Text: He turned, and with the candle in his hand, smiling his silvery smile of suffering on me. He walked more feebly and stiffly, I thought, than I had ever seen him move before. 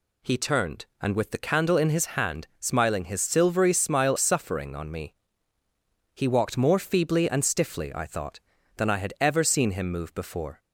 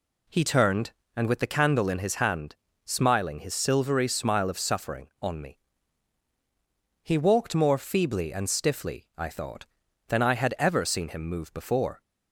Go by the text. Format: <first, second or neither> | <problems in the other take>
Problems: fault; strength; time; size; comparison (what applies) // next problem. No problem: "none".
second | skips "of"; at 4.1 s